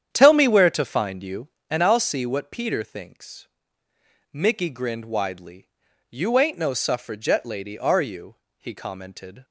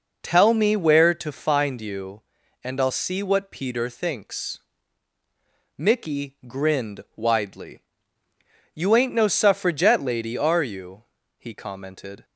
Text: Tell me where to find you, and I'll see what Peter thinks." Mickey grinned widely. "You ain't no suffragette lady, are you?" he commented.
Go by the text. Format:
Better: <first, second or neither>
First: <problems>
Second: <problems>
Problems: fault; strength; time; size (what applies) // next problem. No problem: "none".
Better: second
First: starts louder than the rest; strong; until 1.9 s; 9 dB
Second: none